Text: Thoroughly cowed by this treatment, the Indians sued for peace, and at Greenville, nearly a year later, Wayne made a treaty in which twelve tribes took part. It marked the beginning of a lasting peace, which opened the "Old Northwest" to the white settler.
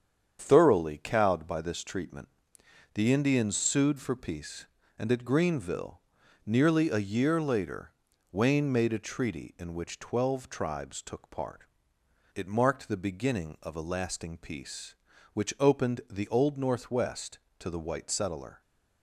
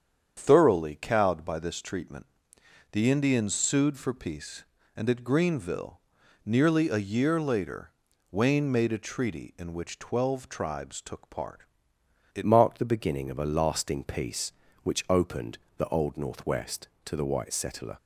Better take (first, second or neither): first